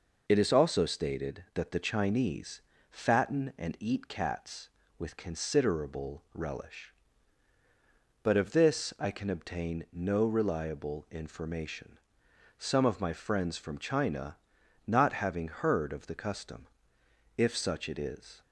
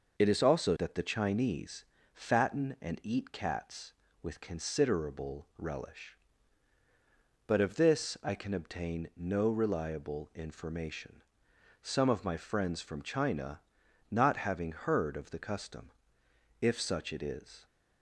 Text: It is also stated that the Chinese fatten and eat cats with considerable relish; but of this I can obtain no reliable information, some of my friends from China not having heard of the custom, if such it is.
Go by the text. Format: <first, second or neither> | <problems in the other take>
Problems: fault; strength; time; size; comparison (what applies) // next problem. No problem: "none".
first | skips "stated"; at 0.7 s // pauses between "Chinese" and "fatten"; slight; at 1.8 s; 0.30 s long; slight in the first // pauses between "China" and "not"; noticeable; at 13.5 s; 0.48 s long; noticeable in the first